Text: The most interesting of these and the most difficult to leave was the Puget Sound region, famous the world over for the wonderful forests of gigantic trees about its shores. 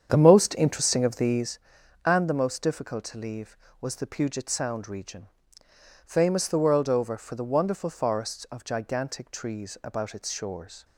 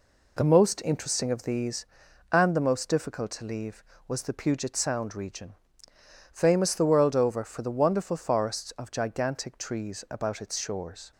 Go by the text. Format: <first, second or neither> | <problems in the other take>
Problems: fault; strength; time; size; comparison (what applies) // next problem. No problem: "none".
second | starts louder than the rest; strong; until 1.5 s; 8 dB